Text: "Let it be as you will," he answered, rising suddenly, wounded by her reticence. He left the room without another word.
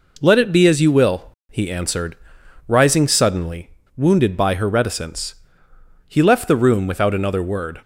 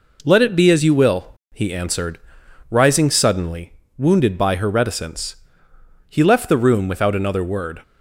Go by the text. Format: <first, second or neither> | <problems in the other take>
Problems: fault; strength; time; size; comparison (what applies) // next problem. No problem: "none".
neither | none